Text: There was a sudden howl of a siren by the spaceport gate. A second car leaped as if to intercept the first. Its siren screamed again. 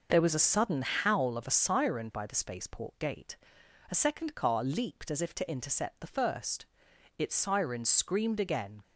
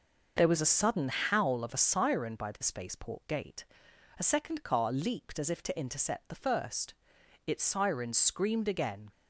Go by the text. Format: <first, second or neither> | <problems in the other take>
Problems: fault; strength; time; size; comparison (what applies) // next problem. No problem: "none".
neither | none